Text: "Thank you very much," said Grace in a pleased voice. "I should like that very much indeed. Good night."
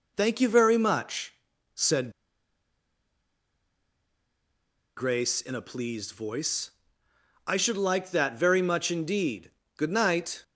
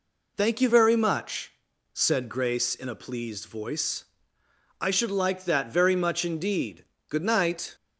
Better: second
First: pauses between "said" and "Grace"; strong; at 2.1 s; 2.8 s long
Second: none

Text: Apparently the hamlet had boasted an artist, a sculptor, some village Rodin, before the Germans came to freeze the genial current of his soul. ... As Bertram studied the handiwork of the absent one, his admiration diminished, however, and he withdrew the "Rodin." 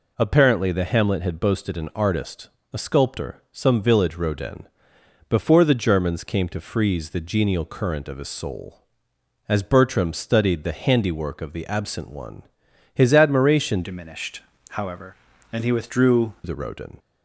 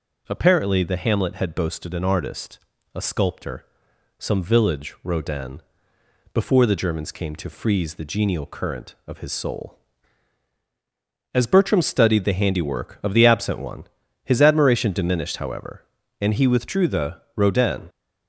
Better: second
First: changes voice from "diminished" to "withdrew"; from 13.8 to 16.3 s; 2.5 s long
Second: none

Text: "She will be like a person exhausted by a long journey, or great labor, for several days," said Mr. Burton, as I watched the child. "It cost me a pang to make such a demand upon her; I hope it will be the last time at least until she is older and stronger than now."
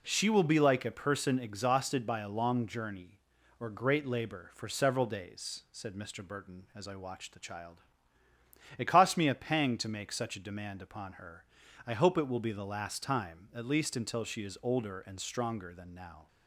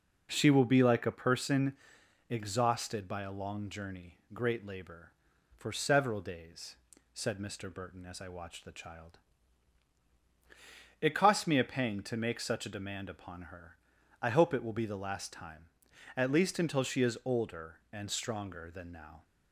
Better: first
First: none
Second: pauses between "person" and "exhausted"; noticeable; at 1.7 s; 0.54 s long // skips "or"; at 4.2 s

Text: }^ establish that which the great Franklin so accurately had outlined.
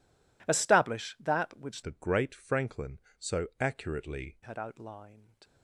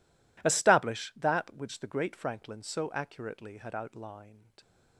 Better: second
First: changes voice from "the" to "accurately"; from 1.8 to 4.3 s; 2.5 s long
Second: none

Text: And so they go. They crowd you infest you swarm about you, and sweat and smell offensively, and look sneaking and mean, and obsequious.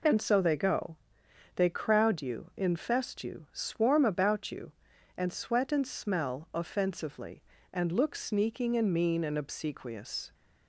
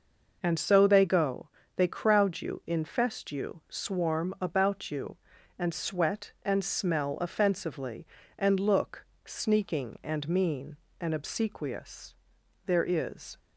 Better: first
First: none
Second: pauses between "look" and "sneaking"; slight; at 9.0 s; 0.22 s long // goes on to say "There is"; noticeable; from 12.6 s on; 0.72 s long

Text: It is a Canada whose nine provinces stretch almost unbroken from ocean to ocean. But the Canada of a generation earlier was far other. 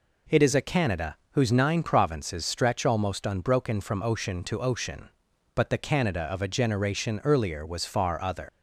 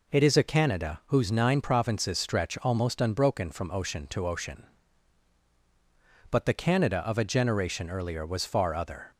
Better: second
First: pauses between "Canada" and "whose"; slight; at 1.1 s; 0.16 s long // leaves "other" unfinished; at 8.4 s; 130 ms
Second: none

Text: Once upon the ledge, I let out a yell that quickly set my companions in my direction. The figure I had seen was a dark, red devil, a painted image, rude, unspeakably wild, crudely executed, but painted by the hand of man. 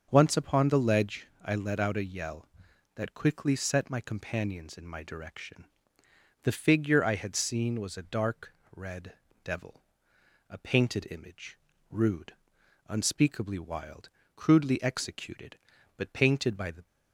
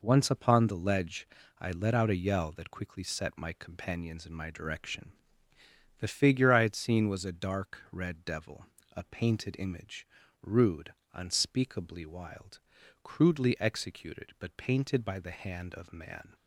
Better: second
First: starts louder than the rest; until 1.1 s; 7 dB // pauses between "red" and "devil"; slight; at 9.1 s; 0.28 s long // stops before "hand of man"; at 16.8 s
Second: none

